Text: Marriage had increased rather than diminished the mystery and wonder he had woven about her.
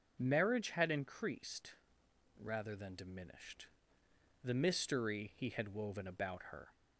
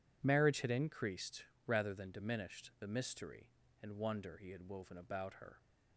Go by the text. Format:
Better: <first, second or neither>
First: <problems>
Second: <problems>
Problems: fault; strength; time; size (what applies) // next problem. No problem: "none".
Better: second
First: pauses between "increased" and "rather"; noticeable; at 1.7 s; 0.66 s long // pauses between "diminished" and "the"; noticeable; at 3.6 s; 0.76 s long // skips "and wonder"; at 5.3 s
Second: pauses between "increased" and "rather"; slight; at 1.4 s; 0.20 s long